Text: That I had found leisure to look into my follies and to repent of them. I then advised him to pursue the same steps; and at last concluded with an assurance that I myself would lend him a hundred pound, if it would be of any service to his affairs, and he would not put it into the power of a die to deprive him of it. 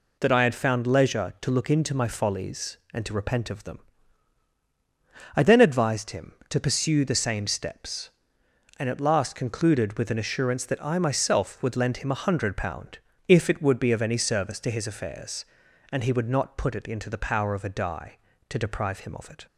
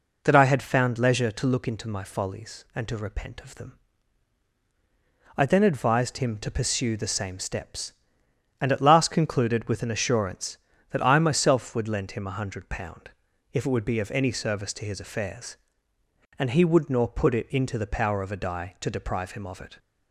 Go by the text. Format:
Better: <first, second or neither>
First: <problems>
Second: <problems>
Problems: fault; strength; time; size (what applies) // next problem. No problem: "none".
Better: first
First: none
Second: says "nor" for "not"; at 16.9 s